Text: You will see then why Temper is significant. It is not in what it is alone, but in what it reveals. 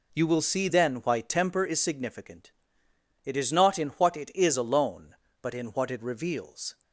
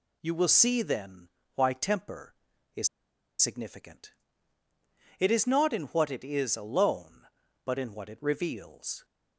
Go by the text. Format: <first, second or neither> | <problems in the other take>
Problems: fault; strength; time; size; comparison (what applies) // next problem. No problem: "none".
first | pauses between "then" and "why"; slight; at 1.2 s; 0.26 s long // pauses between "is" and "significant"; noticeable; at 2.8 s; 0.53 s long